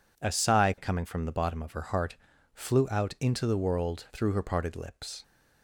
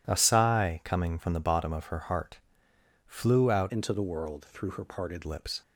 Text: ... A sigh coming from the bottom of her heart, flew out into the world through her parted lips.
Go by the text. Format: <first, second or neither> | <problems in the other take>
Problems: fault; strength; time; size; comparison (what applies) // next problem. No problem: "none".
first | changes voice from "into" to "parted"; from 3.6 to 5.2 s; 1.6 s long